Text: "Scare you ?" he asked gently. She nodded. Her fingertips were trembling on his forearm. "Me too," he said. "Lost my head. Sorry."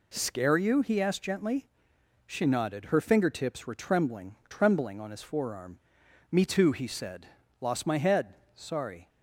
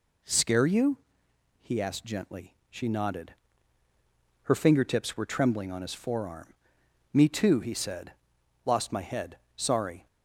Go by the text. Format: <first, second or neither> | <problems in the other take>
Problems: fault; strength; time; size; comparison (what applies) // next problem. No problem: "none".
second | says "trembling" twice; at 4.5 s